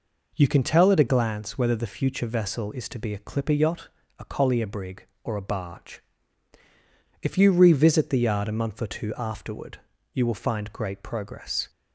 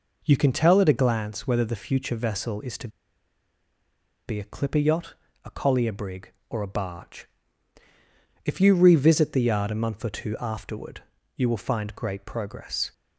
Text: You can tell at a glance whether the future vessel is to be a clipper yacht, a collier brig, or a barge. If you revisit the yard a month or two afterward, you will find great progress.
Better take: first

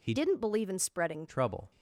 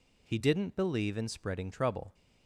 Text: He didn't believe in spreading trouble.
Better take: second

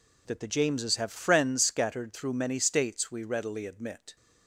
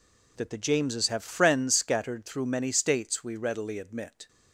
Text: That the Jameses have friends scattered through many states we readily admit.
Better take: neither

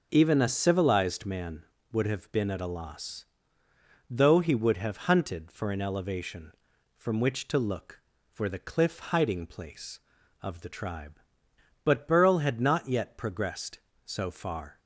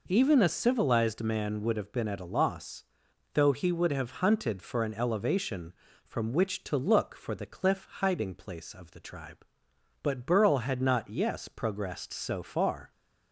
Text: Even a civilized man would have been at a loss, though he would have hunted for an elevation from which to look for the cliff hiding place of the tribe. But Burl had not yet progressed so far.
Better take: first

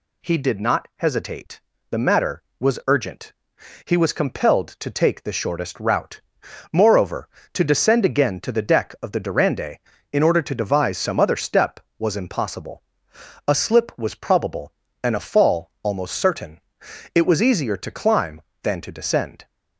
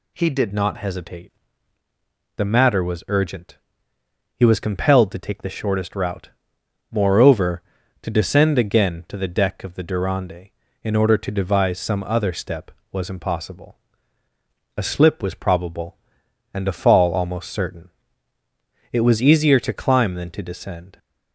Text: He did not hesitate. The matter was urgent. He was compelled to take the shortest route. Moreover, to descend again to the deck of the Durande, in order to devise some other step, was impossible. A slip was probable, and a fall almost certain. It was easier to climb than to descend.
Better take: first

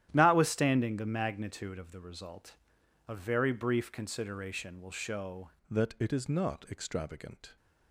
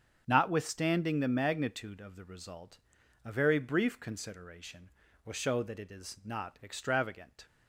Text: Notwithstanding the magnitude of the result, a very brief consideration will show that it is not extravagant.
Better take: second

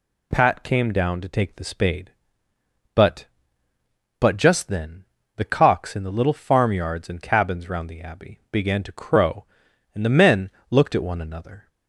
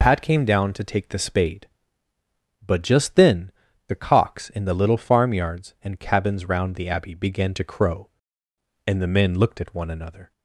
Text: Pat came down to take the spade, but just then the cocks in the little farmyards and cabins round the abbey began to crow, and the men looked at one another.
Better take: second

